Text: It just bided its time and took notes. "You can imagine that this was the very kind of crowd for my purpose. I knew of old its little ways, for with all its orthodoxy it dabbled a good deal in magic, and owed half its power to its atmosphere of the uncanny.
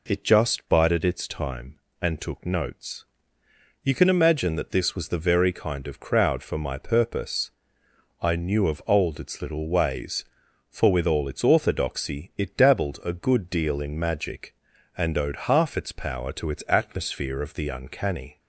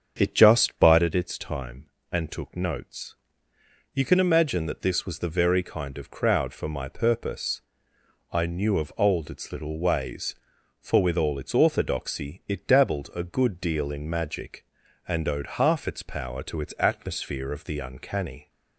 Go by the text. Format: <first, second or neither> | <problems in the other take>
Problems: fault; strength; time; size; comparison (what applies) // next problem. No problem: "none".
first | starts louder than the rest; strong; until 1.1 s; 7.5 dB